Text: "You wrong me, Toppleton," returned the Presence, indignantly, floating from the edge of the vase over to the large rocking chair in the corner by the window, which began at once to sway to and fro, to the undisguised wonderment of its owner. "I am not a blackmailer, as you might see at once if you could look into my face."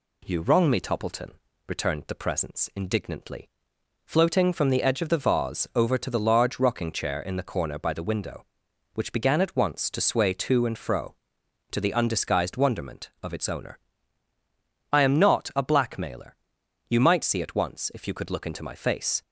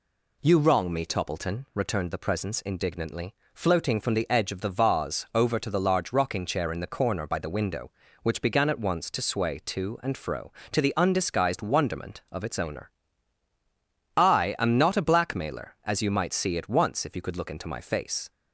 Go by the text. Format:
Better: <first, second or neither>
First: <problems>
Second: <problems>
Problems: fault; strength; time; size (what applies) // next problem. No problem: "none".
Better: second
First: skips "as"; at 16.6 s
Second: none